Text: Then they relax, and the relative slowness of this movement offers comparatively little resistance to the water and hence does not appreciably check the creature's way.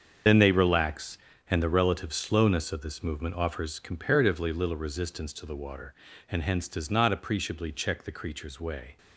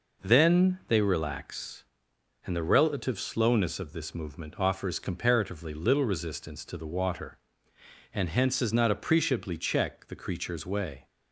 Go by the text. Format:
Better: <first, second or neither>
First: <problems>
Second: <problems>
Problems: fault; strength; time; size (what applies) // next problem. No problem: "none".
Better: second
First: loses the start of "Then"; at 0.2 s; 50 ms // starts louder than the rest; strong; until 1.5 s; 7.5 dB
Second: none